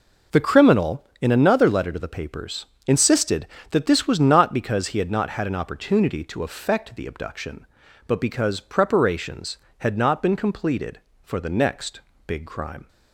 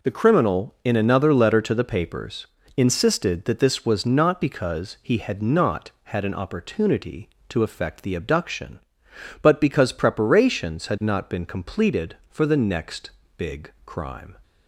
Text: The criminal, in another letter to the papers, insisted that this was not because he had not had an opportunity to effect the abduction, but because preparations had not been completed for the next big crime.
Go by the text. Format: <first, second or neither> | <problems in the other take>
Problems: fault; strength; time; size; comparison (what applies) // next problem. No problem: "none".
neither | pauses between "next" and "big"; slight; the same in both